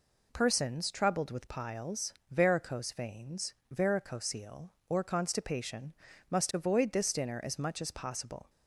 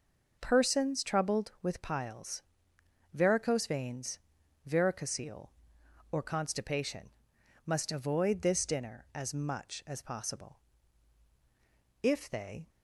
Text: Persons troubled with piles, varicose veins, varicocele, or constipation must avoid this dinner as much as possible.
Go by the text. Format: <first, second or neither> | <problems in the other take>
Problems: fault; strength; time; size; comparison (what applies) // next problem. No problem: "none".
first | pauses between "constipation" and "must"; noticeable; at 7.1 s; 0.54 s long; slight in the first // goes on to say "If they"; noticeable; from 12.0 s on; 0.66 s long